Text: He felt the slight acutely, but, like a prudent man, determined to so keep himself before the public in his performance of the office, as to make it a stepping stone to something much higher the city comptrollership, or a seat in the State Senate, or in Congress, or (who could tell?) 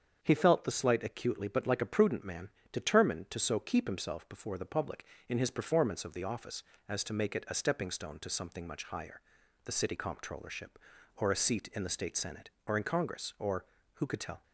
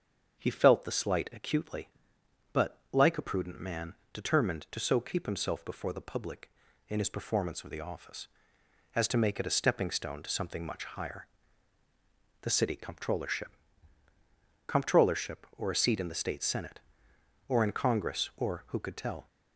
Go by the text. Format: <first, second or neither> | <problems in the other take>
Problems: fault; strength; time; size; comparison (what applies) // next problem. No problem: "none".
first | starts louder than the rest; until 1.4 s; 7 dB; strong in the first // pauses between "higher" and "the"; at 11.2 s; 1.1 s long; also in the first // says "comptrollership" twice; at 14.6 s